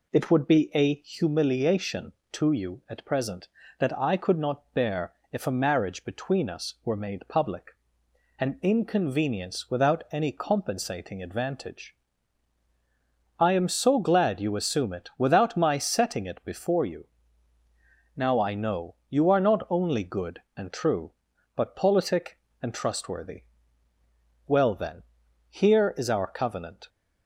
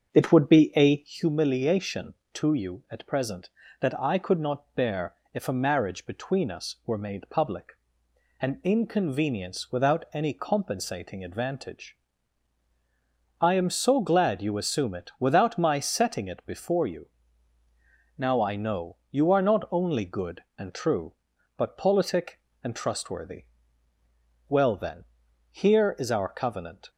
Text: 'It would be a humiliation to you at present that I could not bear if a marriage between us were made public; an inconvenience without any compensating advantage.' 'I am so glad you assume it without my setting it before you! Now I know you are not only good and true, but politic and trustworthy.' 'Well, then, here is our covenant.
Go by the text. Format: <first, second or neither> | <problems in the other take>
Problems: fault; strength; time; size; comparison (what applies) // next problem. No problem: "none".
first | starts louder than the rest; strong; until 1.2 s; 7.5 dB // pauses between "bear" and "if"; slight; at 5.1 s; 0.20 s long; slight in the first // pauses between "know" and "you"; slight; at 18.9 s; 0.16 s long; slight in the first